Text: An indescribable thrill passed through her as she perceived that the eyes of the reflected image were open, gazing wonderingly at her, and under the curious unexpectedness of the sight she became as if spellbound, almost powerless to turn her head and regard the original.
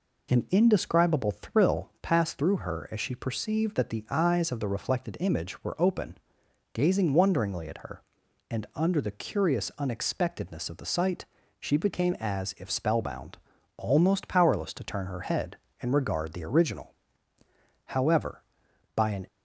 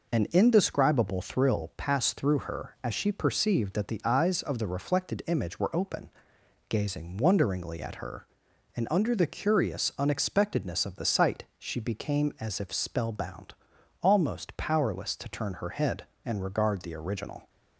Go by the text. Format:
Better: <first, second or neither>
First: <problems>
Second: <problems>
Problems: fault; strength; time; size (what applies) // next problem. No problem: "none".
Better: second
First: pauses between "sight" and "she"; slight; at 11.2 s; 0.34 s long // goes on to say "However by an"; from 17.8 s on; 1.3 s long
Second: none